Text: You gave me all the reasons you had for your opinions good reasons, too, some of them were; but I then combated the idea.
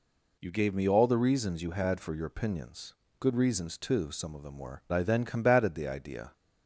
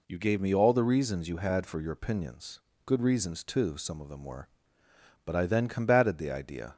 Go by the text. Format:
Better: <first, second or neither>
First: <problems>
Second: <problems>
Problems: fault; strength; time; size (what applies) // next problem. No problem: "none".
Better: second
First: pauses between "opinions" and "good"; slight; at 2.9 s; 0.26 s long // skips "but"; at 4.8 s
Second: pauses between "opinions" and "good"; slight; at 2.5 s; 0.26 s long